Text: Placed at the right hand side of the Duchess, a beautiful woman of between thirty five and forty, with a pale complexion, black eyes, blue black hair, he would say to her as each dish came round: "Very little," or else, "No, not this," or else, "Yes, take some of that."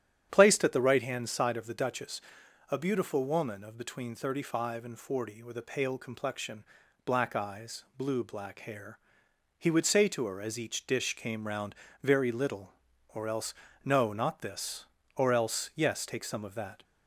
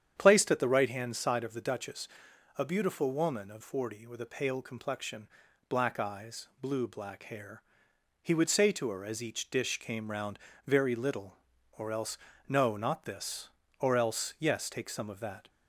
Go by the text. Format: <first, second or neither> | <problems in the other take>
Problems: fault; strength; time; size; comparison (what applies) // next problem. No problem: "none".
first | starts louder than the rest; strong; until 1.1 s; 8.5 dB; strong in the first // skips "between thirty five and"; at 3.6 s